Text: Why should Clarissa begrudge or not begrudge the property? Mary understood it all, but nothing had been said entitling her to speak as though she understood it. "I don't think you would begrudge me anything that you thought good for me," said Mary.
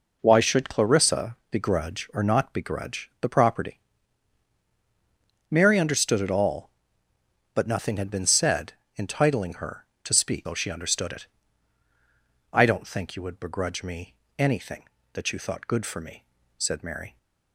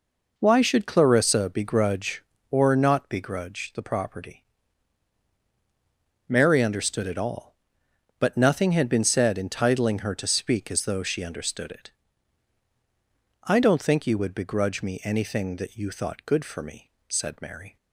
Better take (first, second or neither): second